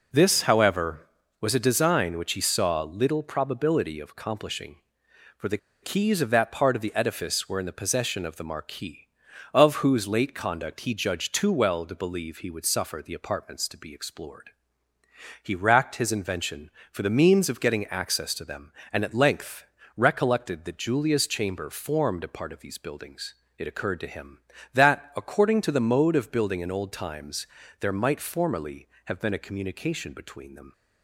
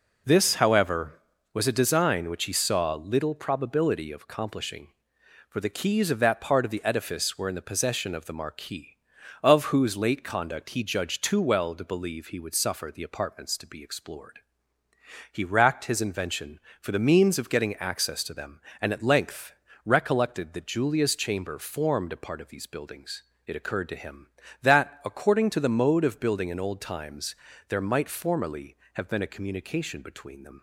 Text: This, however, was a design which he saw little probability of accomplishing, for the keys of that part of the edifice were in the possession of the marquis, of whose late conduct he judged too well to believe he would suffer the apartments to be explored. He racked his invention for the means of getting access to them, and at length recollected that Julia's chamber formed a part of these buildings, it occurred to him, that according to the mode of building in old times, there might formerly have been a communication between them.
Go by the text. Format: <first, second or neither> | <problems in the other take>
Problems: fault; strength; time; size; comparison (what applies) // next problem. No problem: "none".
second | pauses between "the" and "keys"; slight; at 5.5 s; 0.25 s long // pauses between "length" and "recollected"; slight; at 19.6 s; 0.32 s long; slight in the second